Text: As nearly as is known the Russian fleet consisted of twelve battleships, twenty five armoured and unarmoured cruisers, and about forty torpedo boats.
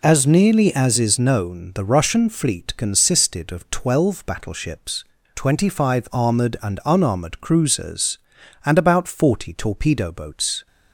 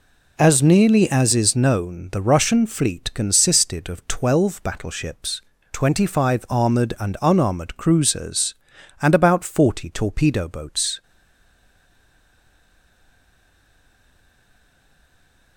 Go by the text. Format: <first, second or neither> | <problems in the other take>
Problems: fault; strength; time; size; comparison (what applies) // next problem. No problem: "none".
first | stays silent after the last word; strong; from 11.0 s on; 4.5 s long